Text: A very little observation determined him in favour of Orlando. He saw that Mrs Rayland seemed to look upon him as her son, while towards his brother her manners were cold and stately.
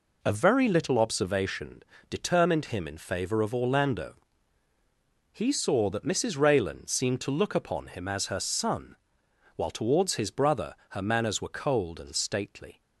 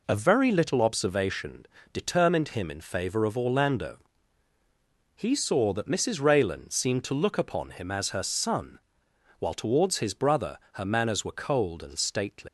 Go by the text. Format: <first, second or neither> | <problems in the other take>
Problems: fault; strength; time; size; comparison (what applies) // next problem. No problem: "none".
first | pauses between "observation" and "determined"; slight; at 1.6 s; 0.30 s long; slight in the first // pauses between "brother" and "her"; slight; at 10.5 s; 0.16 s long; slight in the first // leaves "stately" unfinished; at 12.4 s; 160 ms